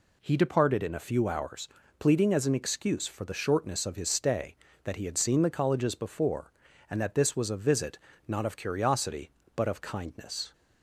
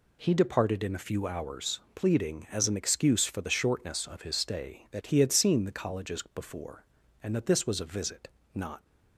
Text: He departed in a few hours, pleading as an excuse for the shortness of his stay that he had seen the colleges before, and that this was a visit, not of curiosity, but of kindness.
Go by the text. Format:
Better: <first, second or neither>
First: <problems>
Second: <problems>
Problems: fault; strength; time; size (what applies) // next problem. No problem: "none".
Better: first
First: none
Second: stops before "of curiosity but of kindness"; at 8.8 s